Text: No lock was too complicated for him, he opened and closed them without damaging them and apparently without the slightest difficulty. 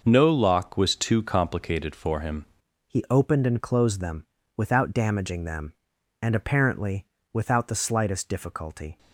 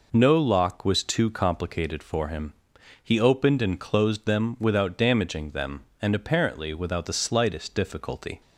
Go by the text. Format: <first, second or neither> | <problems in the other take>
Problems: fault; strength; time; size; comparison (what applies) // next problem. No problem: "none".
second | changes voice at "he"; from 2.8 s on; 6.1 s long // pauses between "them" and "without"; slight; at 4.2 s; 0.30 s long // pauses between "apparently" and "without"; slight; at 7.0 s; 0.26 s long